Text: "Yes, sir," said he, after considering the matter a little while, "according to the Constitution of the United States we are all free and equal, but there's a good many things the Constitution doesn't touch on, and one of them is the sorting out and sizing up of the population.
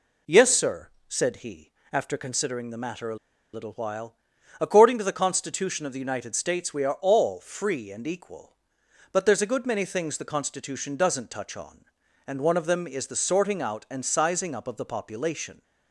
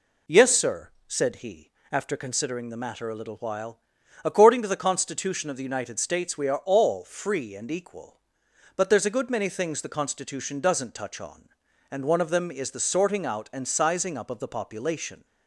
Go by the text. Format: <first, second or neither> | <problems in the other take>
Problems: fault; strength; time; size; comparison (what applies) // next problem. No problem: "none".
second | pauses between "a" and "little"; at 3.1 s; 0.38 s long